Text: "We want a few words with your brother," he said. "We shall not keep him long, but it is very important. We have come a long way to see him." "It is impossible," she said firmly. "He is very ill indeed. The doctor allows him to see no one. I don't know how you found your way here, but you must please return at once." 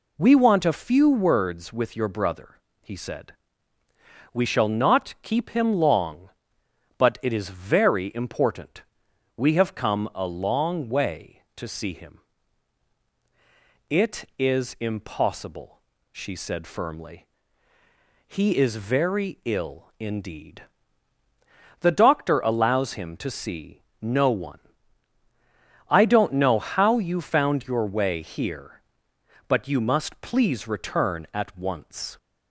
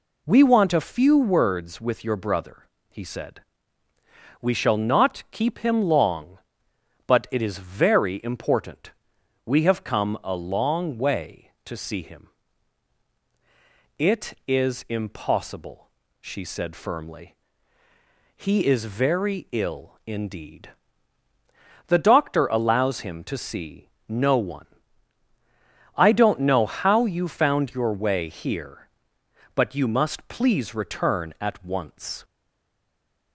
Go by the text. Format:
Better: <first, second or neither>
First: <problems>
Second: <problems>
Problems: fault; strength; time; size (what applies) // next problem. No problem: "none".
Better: first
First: pauses between "see" and "no"; slight; at 23.8 s; 0.20 s long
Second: pauses between "see" and "no"; slight; at 23.8 s; 0.20 s long // stays silent after the last word; from 32.2 s on; 1.1 s long